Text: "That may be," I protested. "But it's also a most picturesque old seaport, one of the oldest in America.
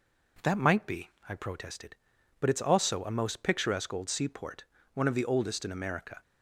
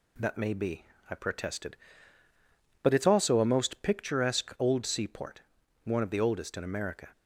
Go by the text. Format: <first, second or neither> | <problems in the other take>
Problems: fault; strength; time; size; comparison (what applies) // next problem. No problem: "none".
second | says "might" for "may"; at 0.5 s